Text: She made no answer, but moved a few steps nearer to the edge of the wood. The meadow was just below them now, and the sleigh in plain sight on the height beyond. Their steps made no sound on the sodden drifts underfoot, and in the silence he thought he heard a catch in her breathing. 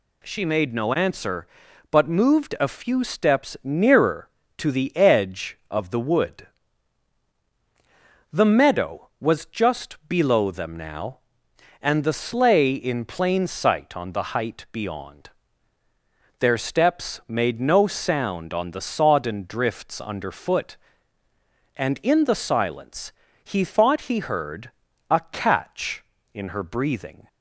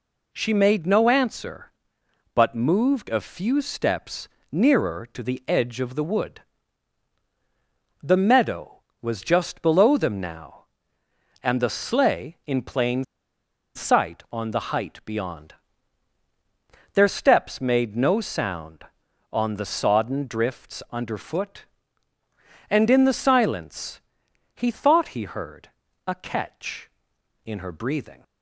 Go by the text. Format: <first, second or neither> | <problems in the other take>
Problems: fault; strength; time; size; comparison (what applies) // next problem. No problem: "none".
first | pauses between "steps" and "nearer"; slight; at 4.2 s; 0.22 s long // pauses between "plain" and "sight"; noticeable; at 13.0 s; 0.70 s long // pauses between "silence" and "he"; noticeable; at 23.9 s; 0.56 s long; slight in the first // pauses between "heard" and "a"; at 25.6 s; 0.38 s long; also in the first